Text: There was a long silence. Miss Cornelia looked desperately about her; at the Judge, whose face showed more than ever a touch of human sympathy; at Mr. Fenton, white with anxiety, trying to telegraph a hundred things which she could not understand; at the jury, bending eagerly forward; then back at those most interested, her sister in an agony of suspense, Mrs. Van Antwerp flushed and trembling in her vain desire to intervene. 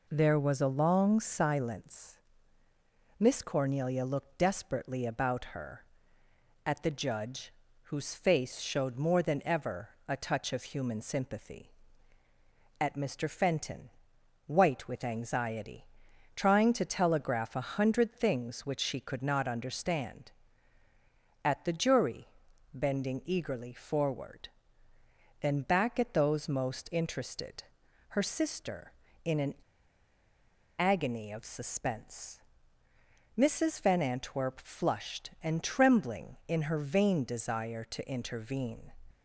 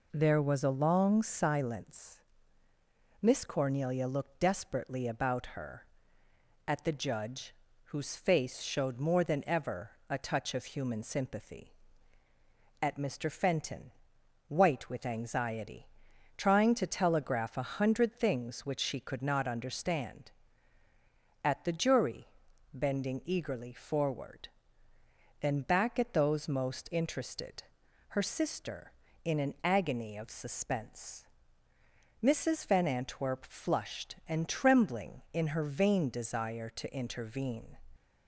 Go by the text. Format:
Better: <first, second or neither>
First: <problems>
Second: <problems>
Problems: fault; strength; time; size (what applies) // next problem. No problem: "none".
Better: second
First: pauses between "ever" and "a"; slight; at 9.8 s; 0.18 s long // pauses between "an" and "agony"; strong; at 29.5 s; 1.2 s long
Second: pauses between "ever" and "a"; slight; at 9.9 s; 0.18 s long